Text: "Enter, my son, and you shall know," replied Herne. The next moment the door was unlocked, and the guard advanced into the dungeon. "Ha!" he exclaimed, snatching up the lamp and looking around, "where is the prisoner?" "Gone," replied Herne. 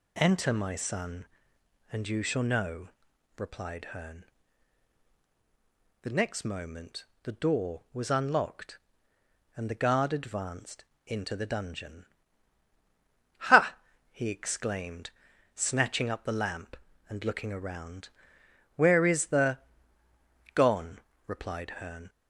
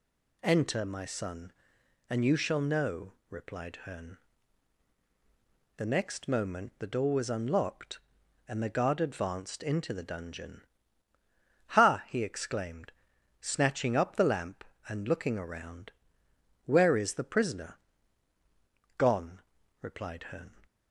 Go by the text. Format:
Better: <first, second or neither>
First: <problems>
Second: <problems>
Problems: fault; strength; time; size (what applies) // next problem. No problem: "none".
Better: second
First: pauses between "moment" and "the"; slight; at 7.0 s; 0.16 s long // pauses between "advanced" and "into"; slight; at 10.8 s; 0.20 s long // skips "prisoner"; at 20.0 s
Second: none